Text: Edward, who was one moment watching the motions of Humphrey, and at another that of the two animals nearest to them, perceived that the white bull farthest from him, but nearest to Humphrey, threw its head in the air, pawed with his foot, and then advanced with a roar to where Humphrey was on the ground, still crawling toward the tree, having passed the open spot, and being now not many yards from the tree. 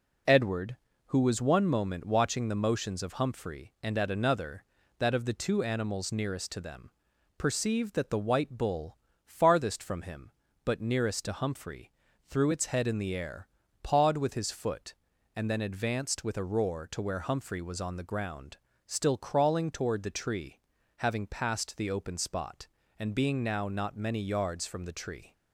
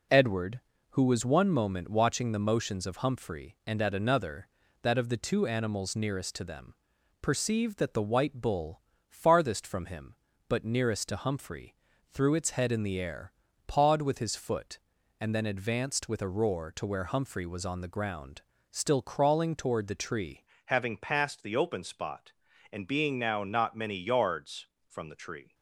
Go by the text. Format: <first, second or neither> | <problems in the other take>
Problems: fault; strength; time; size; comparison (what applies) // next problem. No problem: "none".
first | pauses between "bull" and "farthest"; slight; at 8.8 s; 0.28 s long; slight in the first // changes voice at "having"; from 20.6 s on; 4.9 s long